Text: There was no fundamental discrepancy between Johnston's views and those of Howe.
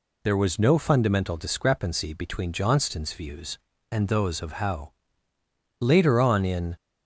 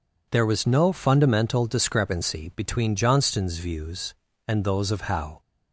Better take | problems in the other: second | goes on to say "Later on in"; noticeable; from 5.7 s on; 0.96 s long

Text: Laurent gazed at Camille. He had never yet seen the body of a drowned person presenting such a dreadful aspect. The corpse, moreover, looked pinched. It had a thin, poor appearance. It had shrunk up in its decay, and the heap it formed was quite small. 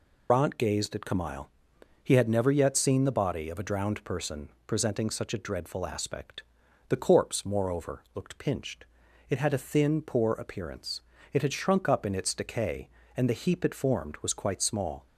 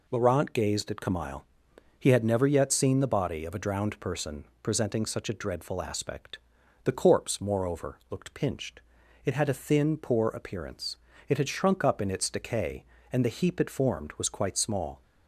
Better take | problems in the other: second | loses the start of "Laurent"; at 0.2 s; 160 ms // pauses between "person" and "presenting"; slight; at 4.4 s; 0.16 s long; slight in the second

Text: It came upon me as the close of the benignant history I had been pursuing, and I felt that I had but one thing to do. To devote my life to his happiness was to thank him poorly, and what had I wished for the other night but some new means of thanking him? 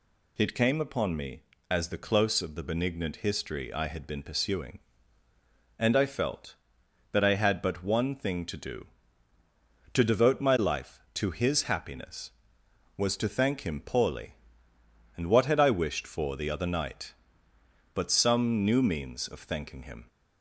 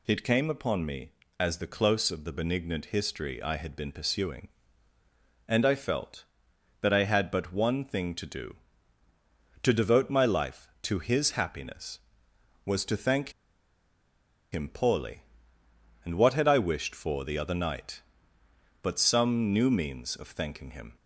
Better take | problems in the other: first | pauses between "thank" and "him"; at 13.3 s; 1.2 s long

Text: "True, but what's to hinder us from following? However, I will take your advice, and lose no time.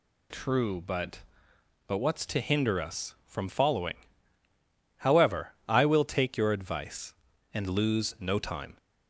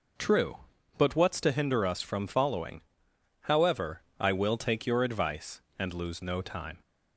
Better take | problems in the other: second | says "but" twice; at 1.8 s

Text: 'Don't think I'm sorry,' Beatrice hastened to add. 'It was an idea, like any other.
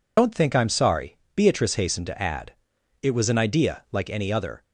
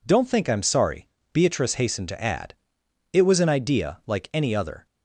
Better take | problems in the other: second | loses the start of "Don't"; at 0.1 s; 70 ms

